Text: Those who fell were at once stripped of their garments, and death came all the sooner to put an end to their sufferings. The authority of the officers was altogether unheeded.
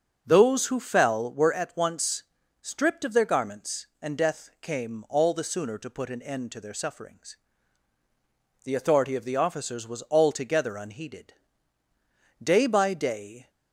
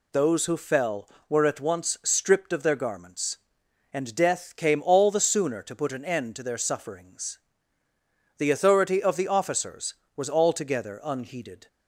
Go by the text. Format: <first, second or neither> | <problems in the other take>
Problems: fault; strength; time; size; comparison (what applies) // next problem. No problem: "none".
second | starts louder than the rest; until 1.2 s; 6.5 dB // pauses between "once" and "stripped"; at 2.2 s; 0.38 s long // goes on to say "Day by day"; noticeable; from 12.4 s on; 1.0 s long